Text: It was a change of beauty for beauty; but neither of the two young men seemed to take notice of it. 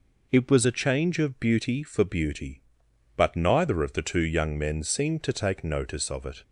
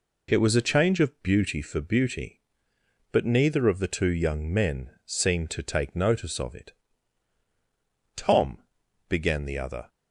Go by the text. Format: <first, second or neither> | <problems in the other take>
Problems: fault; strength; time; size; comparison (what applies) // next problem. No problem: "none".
first | pauses between "men" and "seemed"; slight; at 4.9 s; 0.15 s long // goes on to say "Tom began the other"; from 8.2 s on; 1.6 s long